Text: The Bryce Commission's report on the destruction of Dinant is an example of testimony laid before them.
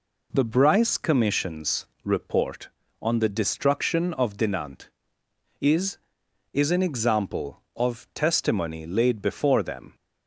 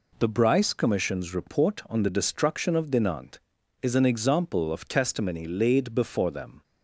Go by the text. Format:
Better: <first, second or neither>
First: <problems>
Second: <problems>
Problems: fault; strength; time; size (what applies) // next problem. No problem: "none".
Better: second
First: pauses between "Commission's" and "report"; slight; at 1.8 s; 0.18 s long // says "is" twice; at 6.5 s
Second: none